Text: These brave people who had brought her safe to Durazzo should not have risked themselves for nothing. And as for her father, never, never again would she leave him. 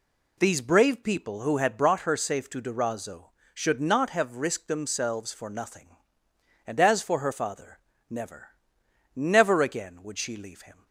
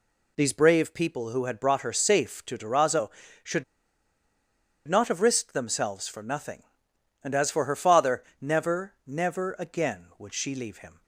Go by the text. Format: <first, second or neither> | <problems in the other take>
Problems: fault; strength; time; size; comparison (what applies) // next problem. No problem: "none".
first | pauses between "should" and "not"; at 3.6 s; 1.2 s long